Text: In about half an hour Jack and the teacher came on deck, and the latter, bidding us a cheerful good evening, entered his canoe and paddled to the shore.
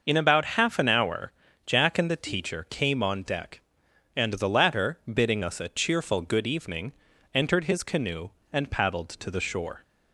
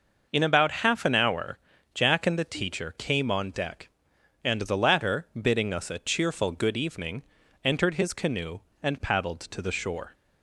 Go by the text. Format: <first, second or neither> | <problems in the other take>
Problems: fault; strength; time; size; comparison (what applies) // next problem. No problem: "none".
neither | pauses between "hour" and "Jack"; the same in both